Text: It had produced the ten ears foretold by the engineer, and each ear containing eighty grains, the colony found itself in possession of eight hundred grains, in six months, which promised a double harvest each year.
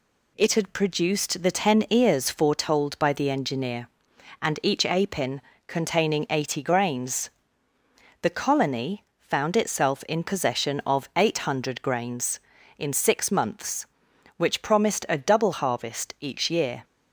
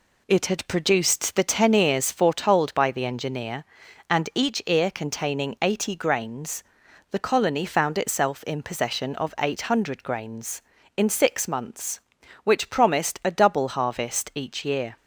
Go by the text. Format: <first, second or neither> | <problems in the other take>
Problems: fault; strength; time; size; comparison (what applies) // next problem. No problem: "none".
second | says "apin" for "ear"; at 4.8 s // pauses between "colony" and "found"; slight; at 9.0 s; 0.16 s long